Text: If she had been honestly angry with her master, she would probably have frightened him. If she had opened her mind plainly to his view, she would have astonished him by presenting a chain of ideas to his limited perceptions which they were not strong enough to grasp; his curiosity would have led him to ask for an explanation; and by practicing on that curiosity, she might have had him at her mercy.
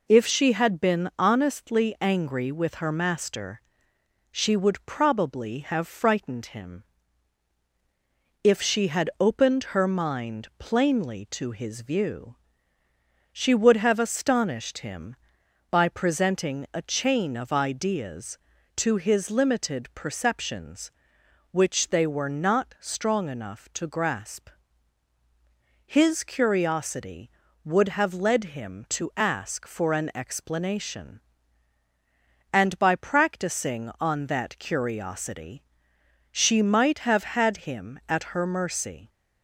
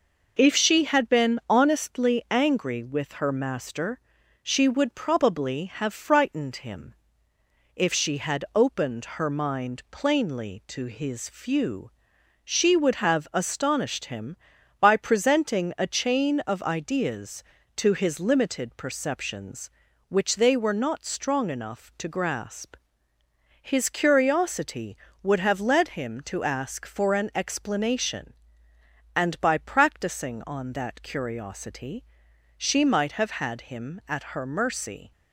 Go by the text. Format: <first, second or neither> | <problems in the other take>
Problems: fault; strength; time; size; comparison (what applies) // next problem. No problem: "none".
first | says "few" for "view"; at 11.2 s